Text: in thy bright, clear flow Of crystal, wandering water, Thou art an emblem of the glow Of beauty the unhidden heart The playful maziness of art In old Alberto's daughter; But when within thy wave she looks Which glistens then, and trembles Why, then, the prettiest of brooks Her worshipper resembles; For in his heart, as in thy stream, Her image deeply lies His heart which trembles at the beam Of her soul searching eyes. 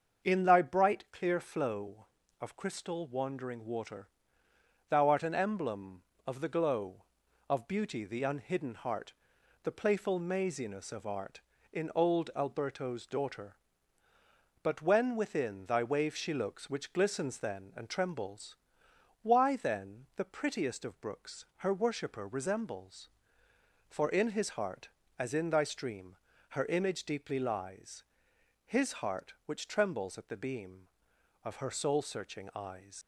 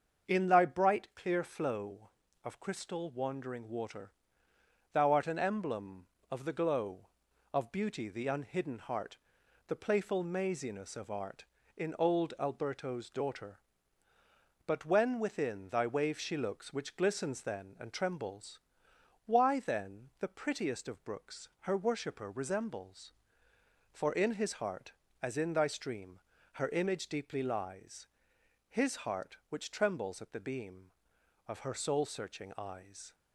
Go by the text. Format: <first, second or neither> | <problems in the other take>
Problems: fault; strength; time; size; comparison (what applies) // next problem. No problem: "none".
second | starts louder than the rest; until 1.3 s; 7 dB; also in the second // pauses between "heart" and "The"; noticeable; at 9.1 s; 0.50 s long; noticeable in the second // pauses between "trembles" and "Why"; noticeable; at 18.5 s; 0.68 s long; noticeable in the second // pauses between "lies" and "His"; noticeable; at 28.0 s; 0.62 s long; noticeable in the second // leaves "eyes" unfinished; at 33.0 s; 105 ms